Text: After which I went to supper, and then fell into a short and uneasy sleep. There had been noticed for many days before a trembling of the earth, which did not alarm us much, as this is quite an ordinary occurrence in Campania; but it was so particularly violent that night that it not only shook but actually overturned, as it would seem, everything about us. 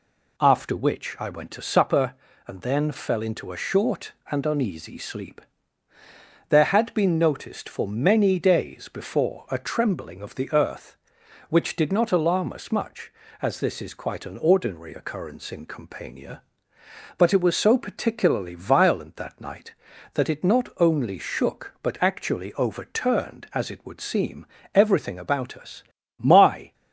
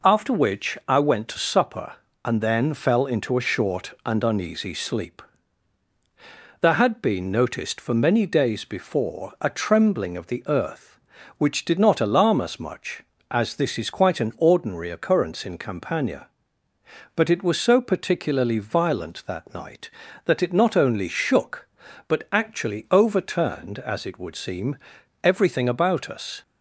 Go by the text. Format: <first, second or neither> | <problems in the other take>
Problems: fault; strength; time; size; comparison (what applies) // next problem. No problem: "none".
second | goes on to say "My"; from 26.1 s on; 0.54 s long